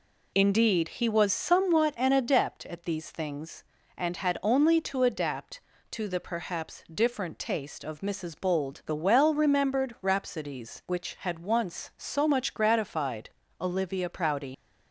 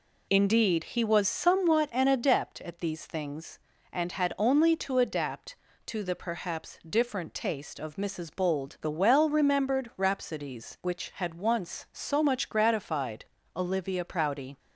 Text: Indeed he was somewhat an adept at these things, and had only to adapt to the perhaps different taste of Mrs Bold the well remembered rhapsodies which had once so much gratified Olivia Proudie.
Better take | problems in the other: second | pauses between "gratified" and "Olivia"; slight; at 13.2 s; 0.32 s long; slight in the second // leaves "Proudie" unfinished; at 14.5 s; 85 ms

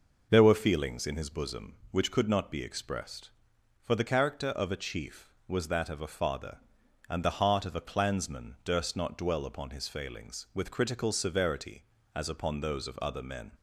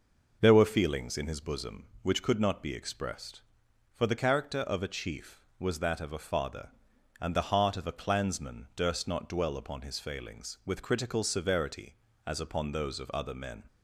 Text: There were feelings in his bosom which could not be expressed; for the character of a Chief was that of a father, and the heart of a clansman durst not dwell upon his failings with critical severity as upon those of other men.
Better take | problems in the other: neither | none

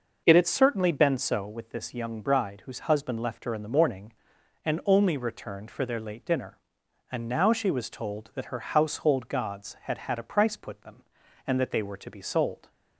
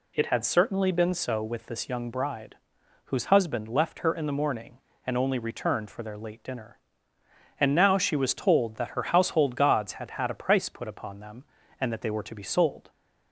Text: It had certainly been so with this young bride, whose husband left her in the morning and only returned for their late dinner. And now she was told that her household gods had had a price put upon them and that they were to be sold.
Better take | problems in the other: second | skips "upon"; at 10.8 s

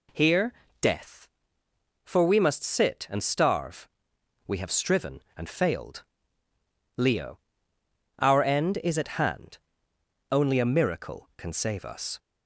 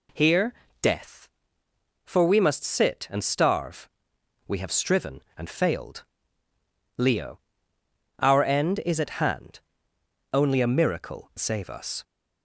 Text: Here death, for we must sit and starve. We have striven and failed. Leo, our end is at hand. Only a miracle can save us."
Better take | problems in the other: first | pauses between "Here" and "death"; slight; at 0.5 s; 0.28 s long; slight in the first // skips "can"; at 11.3 s

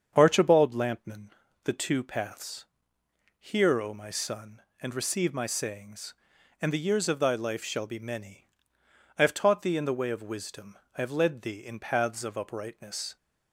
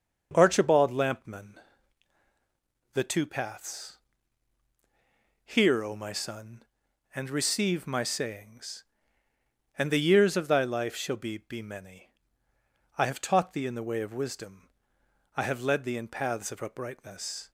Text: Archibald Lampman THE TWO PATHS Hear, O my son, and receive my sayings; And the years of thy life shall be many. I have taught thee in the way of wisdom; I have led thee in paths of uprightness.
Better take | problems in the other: first | starts louder than the rest; noticeable; until 1.3 s; 6 dB; strong in the first // pauses between "Lampman" and "THE"; strong; at 1.5 s; 1.3 s long; slight in the first // pauses between "PATHS" and "Hear"; strong; at 3.9 s; 1.4 s long; noticeable in the first // says "be" twice; at 11.4 s

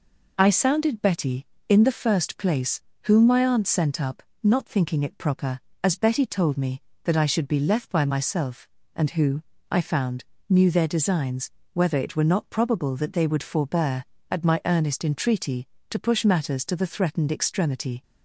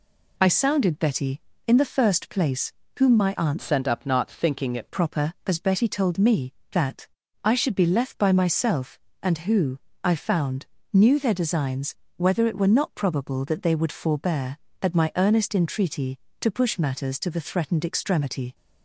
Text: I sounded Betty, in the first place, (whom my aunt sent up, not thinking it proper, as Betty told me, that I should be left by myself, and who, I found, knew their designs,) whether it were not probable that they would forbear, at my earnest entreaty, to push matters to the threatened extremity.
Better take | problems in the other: first | changes voice from "sent" to "it"; from 3.6 to 4.8 s; 1.2 s long // pauses between "that" and "I"; at 7.0 s; 0.38 s long

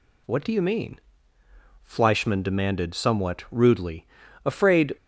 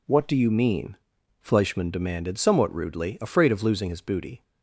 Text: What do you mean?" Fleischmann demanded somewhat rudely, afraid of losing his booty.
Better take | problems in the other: second | stops before "of losing his booty"; at 4.9 s

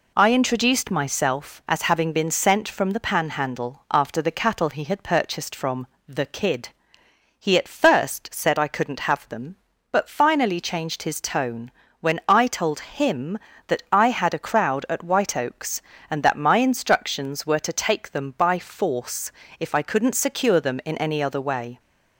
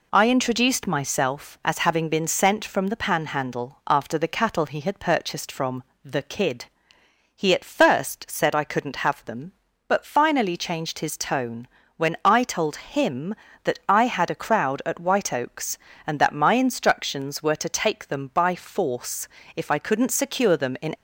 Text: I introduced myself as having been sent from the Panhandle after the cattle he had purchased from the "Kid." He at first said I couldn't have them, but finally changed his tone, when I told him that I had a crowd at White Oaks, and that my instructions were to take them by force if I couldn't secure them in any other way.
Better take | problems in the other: first | pauses between "from" and "the"; slight; at 5.8 s; 0.20 s long; slight in the first // pauses between "force" and "if"; slight; at 19.2 s; 0.28 s long; slight in the first // stops before "any other way"; at 20.9 s

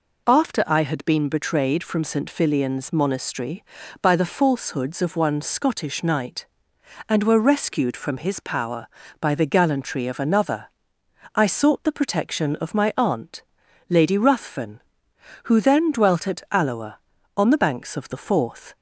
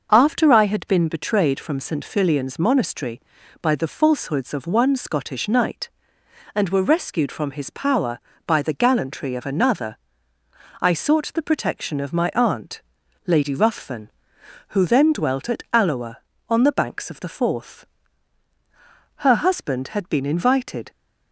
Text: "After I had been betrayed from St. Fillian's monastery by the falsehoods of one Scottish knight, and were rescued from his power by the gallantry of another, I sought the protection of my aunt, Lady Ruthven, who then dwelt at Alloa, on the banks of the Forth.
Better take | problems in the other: first | starts louder than the rest; until 1.1 s; 6 dB // goes on to say "Her husband had been invited"; strong; from 19.1 s on; 1.7 s long

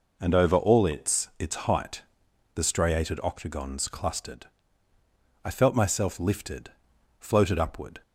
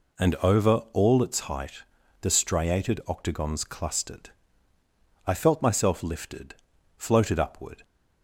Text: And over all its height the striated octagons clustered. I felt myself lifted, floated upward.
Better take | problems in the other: second | says "its" twice; at 1.3 s // pauses between "height" and "the"; noticeable; at 2.0 s; 0.52 s long; also in the second

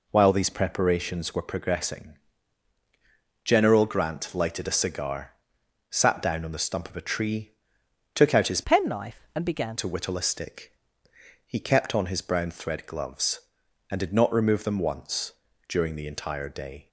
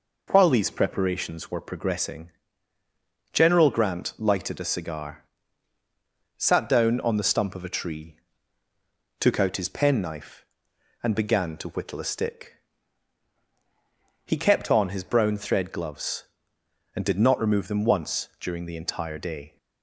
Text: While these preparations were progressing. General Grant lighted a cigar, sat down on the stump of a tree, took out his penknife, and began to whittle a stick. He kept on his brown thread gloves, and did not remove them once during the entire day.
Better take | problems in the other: second | changes voice from "penknife" to "began"; from 8.6 to 9.7 s; 1.1 s long // pauses between "once" and "during"; at 15.3 s; 0.38 s long

